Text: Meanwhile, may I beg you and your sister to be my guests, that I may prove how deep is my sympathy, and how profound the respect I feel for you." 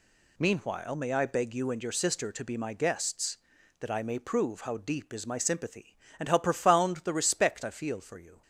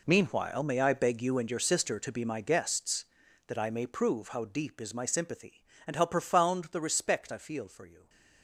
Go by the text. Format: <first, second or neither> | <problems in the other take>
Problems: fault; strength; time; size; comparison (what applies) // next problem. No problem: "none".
first | gets quieter; strong; throughout; 13.5 dB